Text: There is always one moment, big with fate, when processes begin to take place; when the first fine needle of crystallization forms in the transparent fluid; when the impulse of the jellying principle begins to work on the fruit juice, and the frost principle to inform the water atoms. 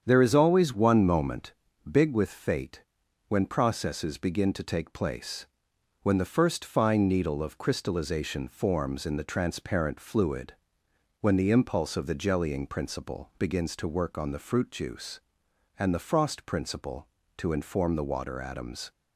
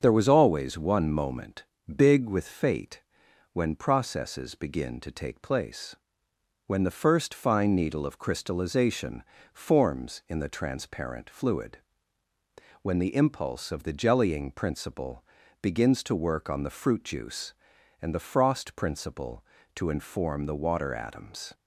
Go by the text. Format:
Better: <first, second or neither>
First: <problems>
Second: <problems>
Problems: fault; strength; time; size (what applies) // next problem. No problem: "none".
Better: first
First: starts louder than the rest; strong; until 1.0 s; 8 dB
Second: starts louder than the rest; until 1.0 s; 7 dB // says "was" for "is"; at 0.2 s // pauses between "crystallization" and "forms"; slight; at 9.2 s; 0.30 s long // pauses between "principle" and "begins"; slight; at 15.2 s; 0.36 s long